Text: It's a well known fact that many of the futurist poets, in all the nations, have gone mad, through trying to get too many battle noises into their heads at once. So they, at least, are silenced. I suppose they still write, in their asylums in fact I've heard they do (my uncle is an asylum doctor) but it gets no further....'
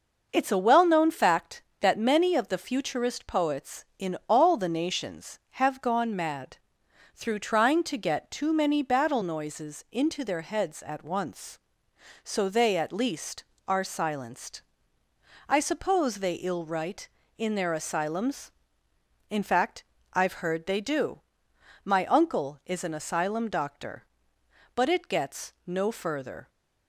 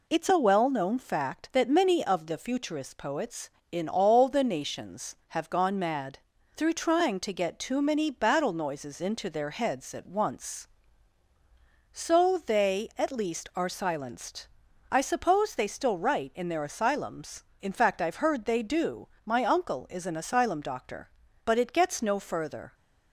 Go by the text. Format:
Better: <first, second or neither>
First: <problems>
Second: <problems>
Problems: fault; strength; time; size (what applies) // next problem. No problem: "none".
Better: second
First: says "ill" for "still"; at 16.3 s // pauses between "fact" and "I've"; slight; at 19.8 s; 0.32 s long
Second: none